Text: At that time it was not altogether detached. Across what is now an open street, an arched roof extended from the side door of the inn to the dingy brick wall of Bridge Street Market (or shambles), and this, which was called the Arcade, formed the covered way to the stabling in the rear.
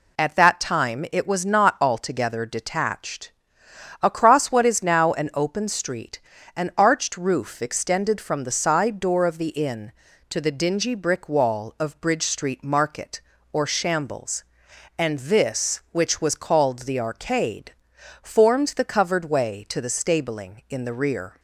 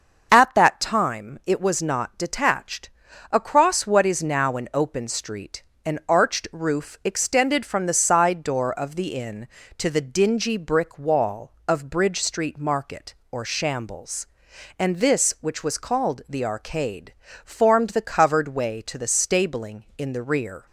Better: first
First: none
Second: starts louder than the rest; until 1.3 s; 6.5 dB // skips "altogether"; at 2.1 s

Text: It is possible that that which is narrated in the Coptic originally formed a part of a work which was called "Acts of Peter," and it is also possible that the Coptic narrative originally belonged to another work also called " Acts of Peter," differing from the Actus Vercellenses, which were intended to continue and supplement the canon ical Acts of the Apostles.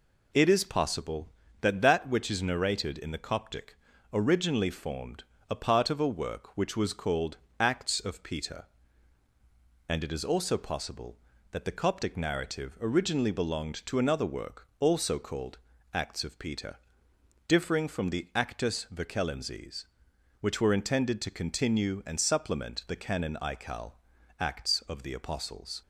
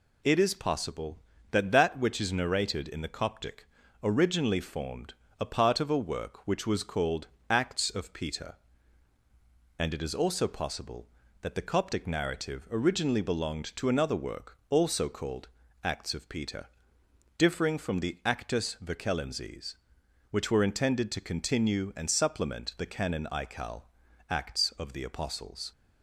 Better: second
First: starts louder than the rest; until 1.4 s; 3.5 dB // pauses between "Coptic" and "originally"; at 3.7 s; 0.38 s long // pauses between "formed" and "a"; slight; at 5.2 s; 0.26 s long // pauses between "called" and "Acts"; slight; at 7.3 s; 0.22 s long // pauses between "ical" and "Acts"; noticeable; at 23.9 s; 0.46 s long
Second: pauses between "Coptic" and "originally"; at 3.6 s; 0.38 s long // pauses between "formed" and "a"; slight; at 5.1 s; 0.26 s long // pauses between "called" and "Acts"; slight; at 7.2 s; 0.22 s long // pauses between "ical" and "Acts"; noticeable; at 23.8 s; 0.46 s long

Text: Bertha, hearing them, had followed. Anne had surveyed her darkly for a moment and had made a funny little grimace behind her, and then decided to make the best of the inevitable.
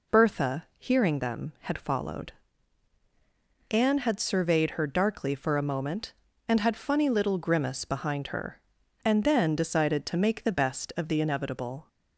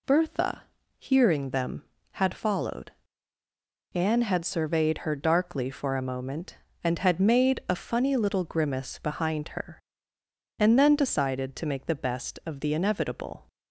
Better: second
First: skips "made a"; at 6.7 s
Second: none

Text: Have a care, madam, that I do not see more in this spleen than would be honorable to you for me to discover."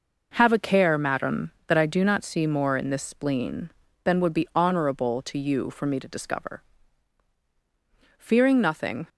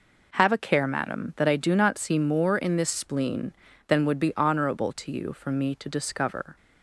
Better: second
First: goes on to say "Fearing nothing"; noticeable; from 8.1 s on; 0.90 s long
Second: none

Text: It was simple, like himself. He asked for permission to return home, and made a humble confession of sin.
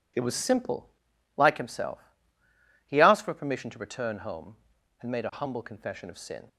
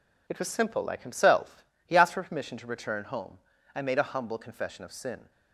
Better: neither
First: none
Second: none

